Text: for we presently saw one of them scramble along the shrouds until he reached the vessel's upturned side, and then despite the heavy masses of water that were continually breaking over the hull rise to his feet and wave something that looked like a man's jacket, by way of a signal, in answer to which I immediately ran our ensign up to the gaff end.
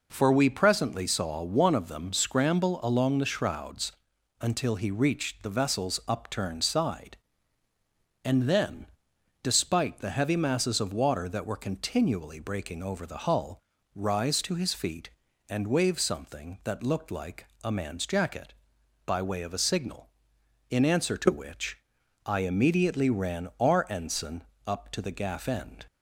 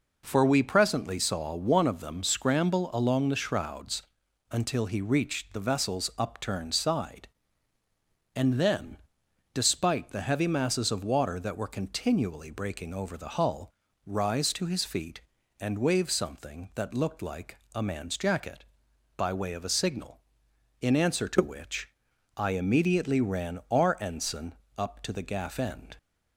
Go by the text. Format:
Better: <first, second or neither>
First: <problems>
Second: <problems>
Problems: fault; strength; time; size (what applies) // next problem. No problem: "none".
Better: neither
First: pauses between "shrouds" and "until"; noticeable; at 3.9 s; 0.48 s long // pauses between "then" and "despite"; noticeable; at 8.8 s; 0.58 s long // pauses between "hull" and "rise"; slight; at 13.6 s; 0.34 s long // pauses between "like" and "a"; slight; at 17.4 s; 0.16 s long // pauses between "which" and "I"; noticeable; at 21.7 s; 0.48 s long // pauses between "ensign" and "up"; slight; at 24.4 s; 0.24 s long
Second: pauses between "shrouds" and "until"; noticeable; at 4.0 s; 0.48 s long // pauses between "then" and "despite"; noticeable; at 8.9 s; 0.58 s long // pauses between "hull" and "rise"; slight; at 13.7 s; 0.34 s long // pauses between "like" and "a"; slight; at 17.5 s; 0.16 s long // pauses between "which" and "I"; noticeable; at 21.8 s; 0.48 s long // pauses between "ensign" and "up"; slight; at 24.5 s; 0.24 s long